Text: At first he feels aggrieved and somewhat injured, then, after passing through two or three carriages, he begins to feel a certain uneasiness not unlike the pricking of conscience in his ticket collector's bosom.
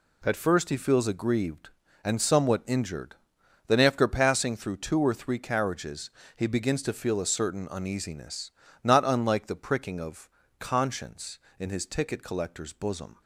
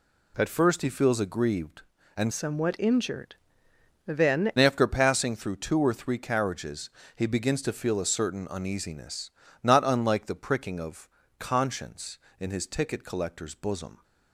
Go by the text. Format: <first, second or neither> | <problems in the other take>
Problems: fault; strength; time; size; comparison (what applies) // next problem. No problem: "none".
first | changes voice from "somewhat" to "then"; from 2.3 to 4.5 s; 2.2 s long // pauses between "uneasiness" and "not"; slight; at 9.3 s; 0.32 s long; slight in the first // pauses between "of" and "conscience"; slight; at 11.0 s; 0.30 s long; slight in the first